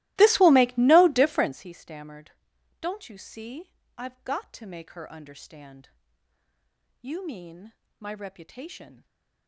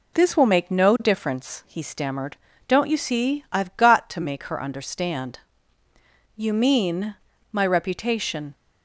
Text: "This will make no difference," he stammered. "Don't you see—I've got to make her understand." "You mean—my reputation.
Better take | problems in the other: second | starts louder than the rest; strong; until 1.7 s; 18.5 dB // stays silent after the last word; slight; from 8.9 s on; 0.5 s long

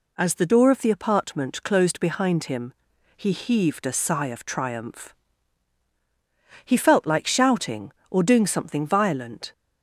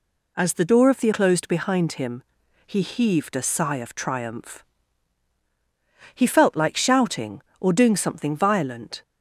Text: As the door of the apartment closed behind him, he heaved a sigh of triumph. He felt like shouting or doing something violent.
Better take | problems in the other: first | skips "apartment"; at 1.1 s

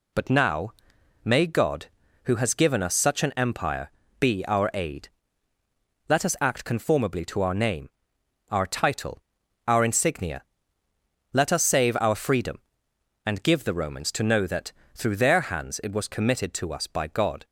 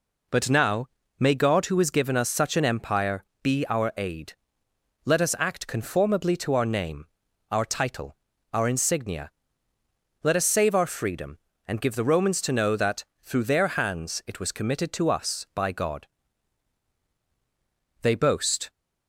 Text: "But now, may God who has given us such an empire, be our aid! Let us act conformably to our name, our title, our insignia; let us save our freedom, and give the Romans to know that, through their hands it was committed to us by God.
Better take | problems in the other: first | goes on to say "They boast"; noticeable; from 18.0 s on; 0.66 s long

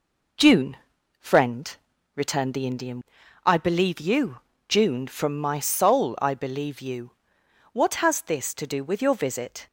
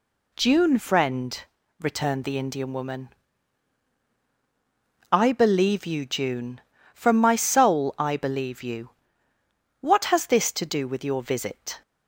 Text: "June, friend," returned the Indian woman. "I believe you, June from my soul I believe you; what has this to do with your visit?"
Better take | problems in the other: second | skips "woman"; at 3.2 s

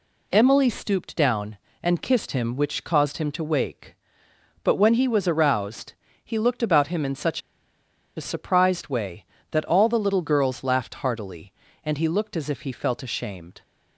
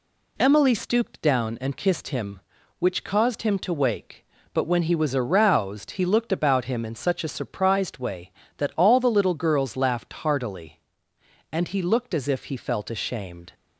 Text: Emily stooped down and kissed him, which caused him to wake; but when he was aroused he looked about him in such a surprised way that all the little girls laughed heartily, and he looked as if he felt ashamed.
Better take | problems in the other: second | pauses between "aroused" and "he"; slight; at 5.9 s; 0.30 s long // pauses between "such" and "a"; noticeable; at 7.4 s; 0.77 s long

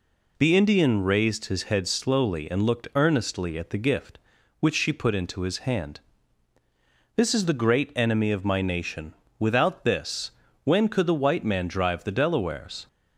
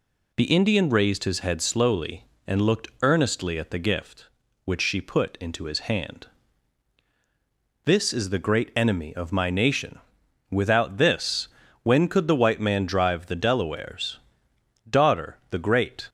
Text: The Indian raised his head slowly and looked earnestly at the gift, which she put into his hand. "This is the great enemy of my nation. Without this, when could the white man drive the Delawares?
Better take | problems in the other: first | goes on to say "Daughter the Great"; noticeable; from 14.8 s on; 1.2 s long

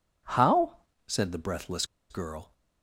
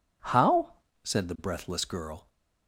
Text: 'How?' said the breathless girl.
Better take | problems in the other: second | pauses between "breathless" and "girl"; slight; at 1.8 s; 0.26 s long

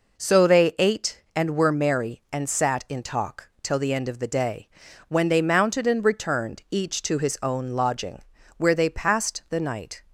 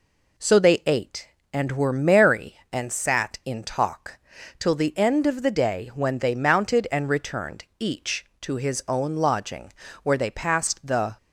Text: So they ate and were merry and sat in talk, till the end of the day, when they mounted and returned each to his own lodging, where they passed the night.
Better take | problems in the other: first | stops before "night"; at 11.1 s

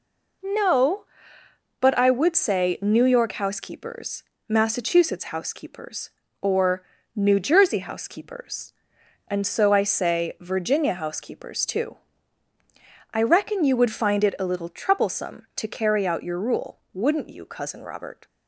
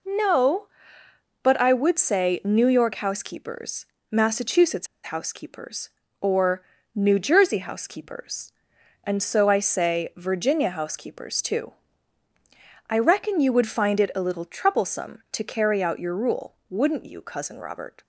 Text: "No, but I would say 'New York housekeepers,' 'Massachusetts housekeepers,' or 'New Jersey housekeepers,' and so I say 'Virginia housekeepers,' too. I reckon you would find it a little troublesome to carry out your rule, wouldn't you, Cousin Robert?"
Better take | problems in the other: first | pauses between "Massachusetts" and "housekeepers"; slight; at 4.8 s; 0.16 s long // pauses between "or" and "New"; slight; at 6.6 s; 0.30 s long; slight in the first

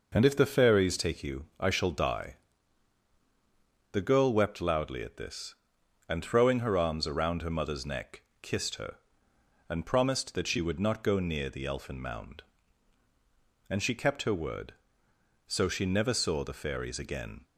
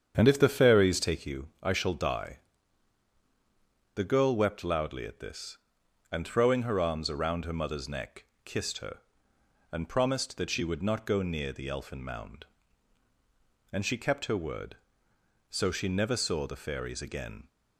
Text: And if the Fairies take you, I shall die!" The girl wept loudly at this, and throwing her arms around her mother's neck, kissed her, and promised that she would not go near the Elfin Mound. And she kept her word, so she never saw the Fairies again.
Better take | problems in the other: first | starts louder than the rest; strong; until 1.4 s; 8 dB

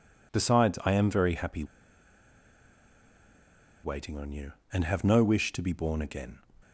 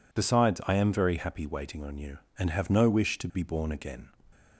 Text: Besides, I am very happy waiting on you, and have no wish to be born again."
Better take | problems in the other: second | pauses between "happy" and "waiting"; strong; at 1.6 s; 2.1 s long

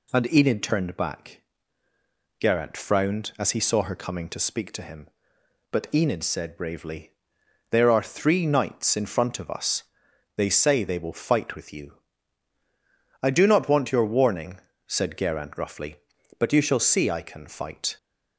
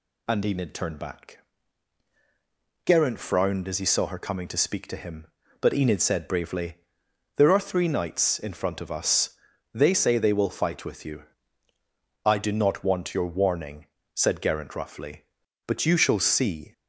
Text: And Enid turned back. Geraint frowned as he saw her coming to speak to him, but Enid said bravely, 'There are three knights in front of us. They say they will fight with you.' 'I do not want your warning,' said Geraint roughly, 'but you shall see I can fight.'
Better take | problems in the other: first | stops before "I can fight"; at 16.7 s

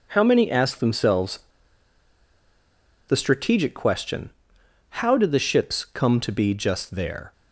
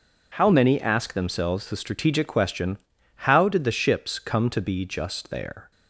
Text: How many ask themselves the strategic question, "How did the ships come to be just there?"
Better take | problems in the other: second | pauses between "themselves" and "the"; strong; at 1.3 s; 1.6 s long

